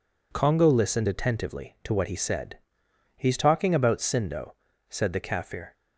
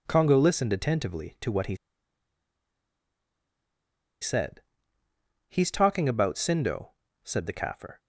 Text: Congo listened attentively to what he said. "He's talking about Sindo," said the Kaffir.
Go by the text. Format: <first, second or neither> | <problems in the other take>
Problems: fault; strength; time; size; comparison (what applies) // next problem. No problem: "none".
first | pauses between "he" and "said"; strong; at 1.7 s; 2.4 s long